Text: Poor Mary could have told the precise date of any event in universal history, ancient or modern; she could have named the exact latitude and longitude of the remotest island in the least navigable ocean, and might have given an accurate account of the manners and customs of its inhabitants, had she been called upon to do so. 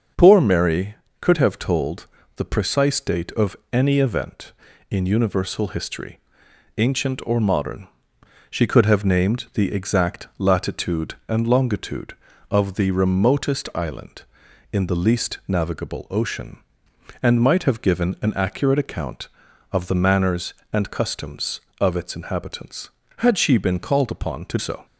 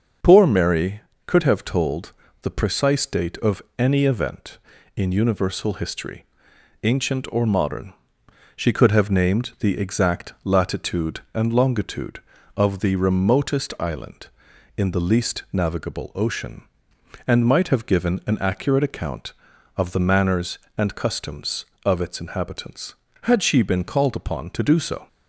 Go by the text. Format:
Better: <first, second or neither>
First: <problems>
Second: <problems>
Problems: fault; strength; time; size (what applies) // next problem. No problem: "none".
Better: second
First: starts louder than the rest; until 1.4 s; 6.5 dB // pauses between "told" and "the"; slight; at 2.0 s; 0.30 s long // pauses between "of" and "any"; slight; at 3.5 s; 0.16 s long // skips "do"; at 24.5 s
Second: starts louder than the rest; until 1.4 s; 6.5 dB // pauses between "told" and "the"; slight; at 2.1 s; 0.30 s long // pauses between "of" and "any"; slight; at 3.6 s; 0.16 s long